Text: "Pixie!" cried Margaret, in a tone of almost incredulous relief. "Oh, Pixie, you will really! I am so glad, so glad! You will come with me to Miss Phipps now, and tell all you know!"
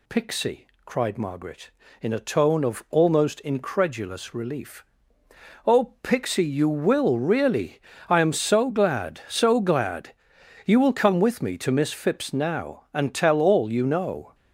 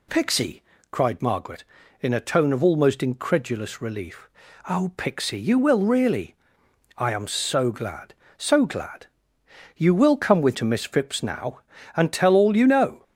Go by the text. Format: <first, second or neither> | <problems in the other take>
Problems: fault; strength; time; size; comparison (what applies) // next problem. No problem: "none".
first | skips "me"; at 10.5 s